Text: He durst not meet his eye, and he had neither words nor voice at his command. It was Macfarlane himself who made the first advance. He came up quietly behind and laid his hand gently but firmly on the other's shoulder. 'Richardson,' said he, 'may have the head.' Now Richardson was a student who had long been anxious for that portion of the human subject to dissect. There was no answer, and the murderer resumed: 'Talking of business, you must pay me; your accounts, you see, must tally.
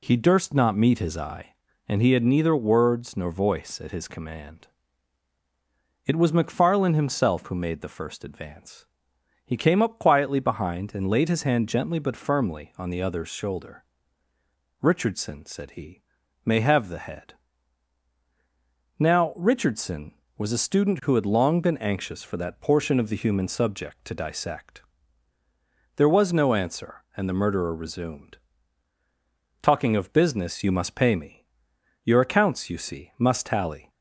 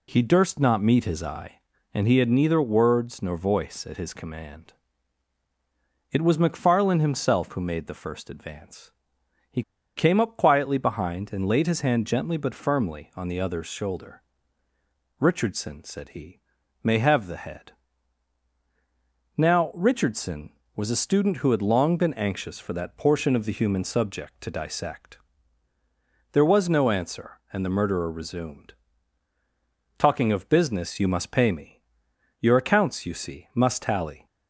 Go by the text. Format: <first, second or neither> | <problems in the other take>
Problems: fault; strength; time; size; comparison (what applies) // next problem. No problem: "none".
first | pauses between "He" and "came"; slight; at 9.6 s; 0.35 s long